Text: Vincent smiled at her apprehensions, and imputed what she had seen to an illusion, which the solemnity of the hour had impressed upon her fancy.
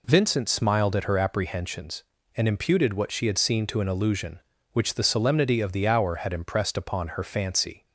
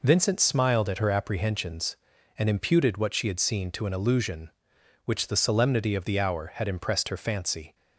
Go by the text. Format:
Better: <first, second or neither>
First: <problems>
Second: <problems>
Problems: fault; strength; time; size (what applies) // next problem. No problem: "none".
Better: first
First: none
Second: skips "upon"; at 7.0 s